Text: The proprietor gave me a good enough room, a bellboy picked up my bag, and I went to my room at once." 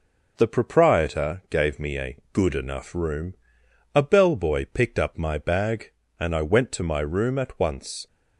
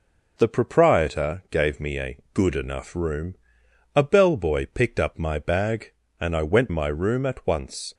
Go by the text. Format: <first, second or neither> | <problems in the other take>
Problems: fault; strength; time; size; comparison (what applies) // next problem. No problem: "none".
first | skips "to"; at 6.6 s